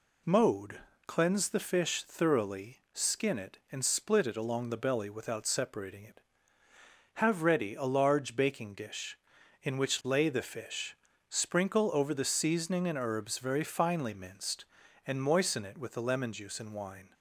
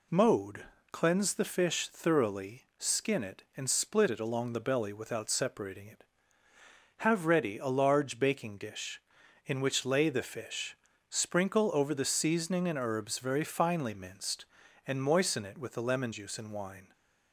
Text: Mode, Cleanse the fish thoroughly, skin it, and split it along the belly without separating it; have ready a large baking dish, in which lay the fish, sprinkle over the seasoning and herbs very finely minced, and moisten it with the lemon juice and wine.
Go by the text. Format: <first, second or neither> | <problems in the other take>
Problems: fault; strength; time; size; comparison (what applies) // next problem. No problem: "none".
neither | none